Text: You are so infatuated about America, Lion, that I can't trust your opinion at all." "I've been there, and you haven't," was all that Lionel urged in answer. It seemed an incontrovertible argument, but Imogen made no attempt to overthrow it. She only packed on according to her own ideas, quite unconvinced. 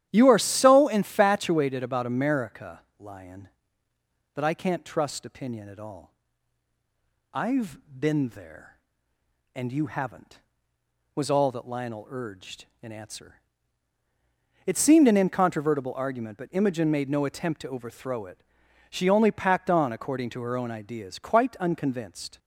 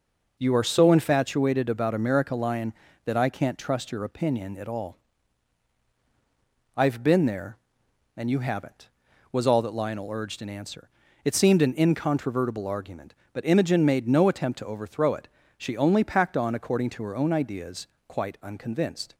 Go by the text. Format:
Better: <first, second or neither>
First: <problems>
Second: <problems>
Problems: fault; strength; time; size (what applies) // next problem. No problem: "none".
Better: second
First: starts louder than the rest; strong; until 1.1 s; 12 dB // skips "your"; at 5.2 s // pauses between "I've" and "been"; slight; at 7.7 s; 0.22 s long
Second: none